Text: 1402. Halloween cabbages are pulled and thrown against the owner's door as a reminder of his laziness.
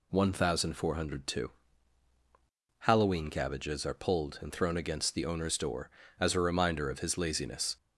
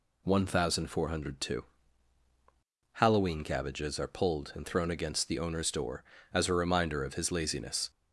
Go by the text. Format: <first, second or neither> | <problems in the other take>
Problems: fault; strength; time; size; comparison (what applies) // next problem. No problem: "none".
neither | none